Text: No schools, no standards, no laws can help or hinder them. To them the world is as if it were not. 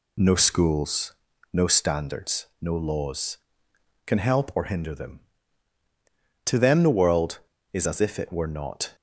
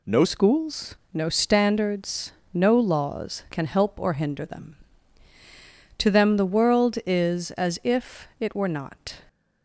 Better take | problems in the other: first | changes voice at "schools"; from 0.2 s on; 9.0 s long

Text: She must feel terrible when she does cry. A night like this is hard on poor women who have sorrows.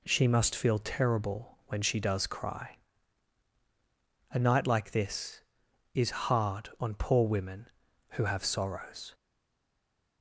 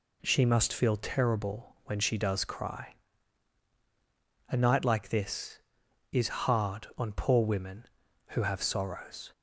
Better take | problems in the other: second | stays silent after the last word; from 9.1 s on; 1.1 s long

